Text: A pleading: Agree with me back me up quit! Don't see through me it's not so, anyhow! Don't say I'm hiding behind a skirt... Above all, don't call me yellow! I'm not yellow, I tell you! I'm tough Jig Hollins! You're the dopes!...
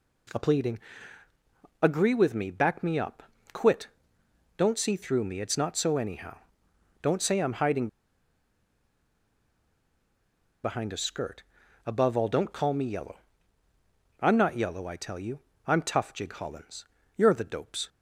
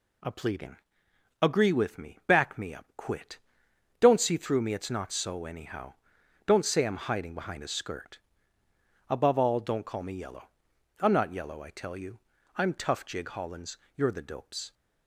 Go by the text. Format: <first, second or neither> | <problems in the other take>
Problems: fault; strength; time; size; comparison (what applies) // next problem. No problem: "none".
second | pauses between "up" and "quit"; slight; at 3.2 s; 0.32 s long // pauses between "hiding" and "behind"; strong; at 7.8 s; 2.7 s long